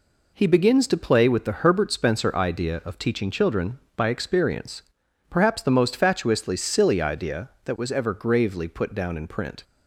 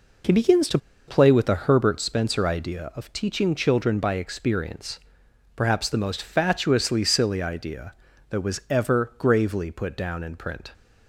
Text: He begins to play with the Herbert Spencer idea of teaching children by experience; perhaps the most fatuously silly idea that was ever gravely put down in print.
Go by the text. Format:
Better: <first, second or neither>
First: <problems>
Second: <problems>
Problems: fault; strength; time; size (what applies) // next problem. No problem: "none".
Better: first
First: none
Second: pauses between "to" and "play"; slight; at 0.7 s; 0.28 s long